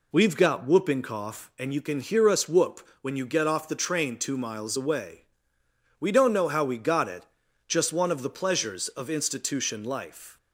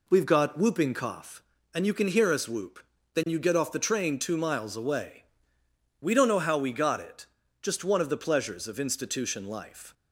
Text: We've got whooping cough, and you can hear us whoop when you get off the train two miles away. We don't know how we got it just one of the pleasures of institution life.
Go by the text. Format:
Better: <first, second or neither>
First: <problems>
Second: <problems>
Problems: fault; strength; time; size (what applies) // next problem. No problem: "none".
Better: first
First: pauses between "it" and "just"; at 7.2 s; 0.44 s long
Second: says "then" for "when"; at 3.1 s // pauses between "it" and "just"; slight; at 7.2 s; 0.36 s long